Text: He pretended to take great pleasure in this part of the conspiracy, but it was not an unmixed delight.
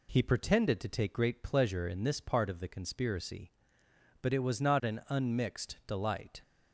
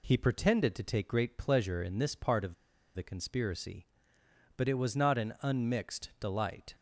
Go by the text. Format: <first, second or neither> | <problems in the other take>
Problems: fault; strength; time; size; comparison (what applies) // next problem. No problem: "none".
first | pauses between "of" and "the"; at 2.5 s; 0.42 s long